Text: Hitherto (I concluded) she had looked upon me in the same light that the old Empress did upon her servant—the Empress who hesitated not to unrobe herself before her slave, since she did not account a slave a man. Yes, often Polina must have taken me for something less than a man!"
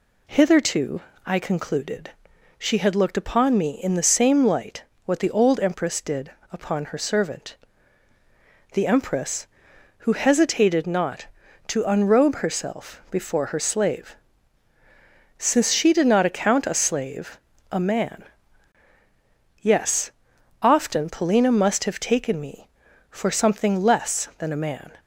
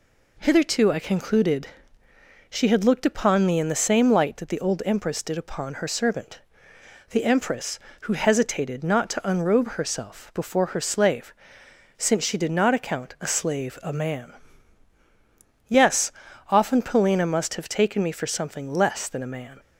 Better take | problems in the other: second | says "what" for "that"; at 5.0 s // pauses between "did" and "upon"; slight; at 6.2 s; 0.22 s long // pauses between "slave" and "a"; slight; at 17.3 s; 0.32 s long

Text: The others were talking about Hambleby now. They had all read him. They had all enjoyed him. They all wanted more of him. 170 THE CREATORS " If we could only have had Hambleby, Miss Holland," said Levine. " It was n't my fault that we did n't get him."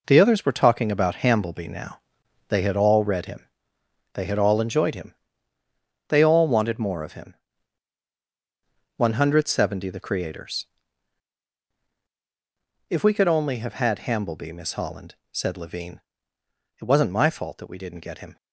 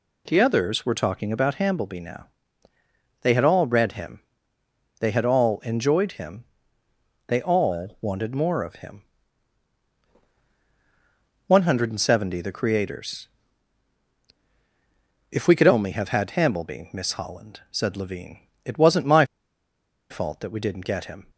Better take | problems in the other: first | pauses between "my" and "fault"; noticeable; at 19.2 s; 0.85 s long

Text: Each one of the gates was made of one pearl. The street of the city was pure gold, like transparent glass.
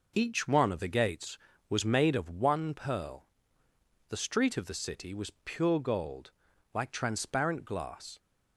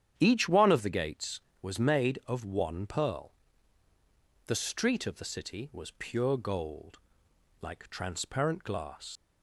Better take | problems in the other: first | starts louder than the rest; strong; until 1.1 s; 9.5 dB // leaves "glass" unfinished; at 9.1 s; 105 ms

